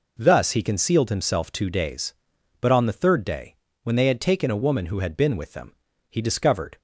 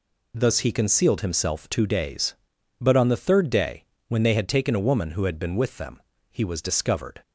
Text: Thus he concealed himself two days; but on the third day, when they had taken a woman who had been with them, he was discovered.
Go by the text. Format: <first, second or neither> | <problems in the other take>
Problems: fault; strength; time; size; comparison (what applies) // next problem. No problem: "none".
second | skips "was"; at 6.2 s